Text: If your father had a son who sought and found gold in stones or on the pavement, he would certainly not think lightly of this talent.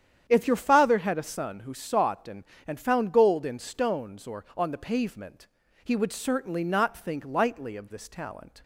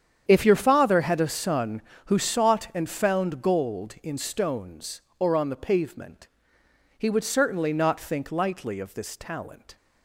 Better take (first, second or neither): second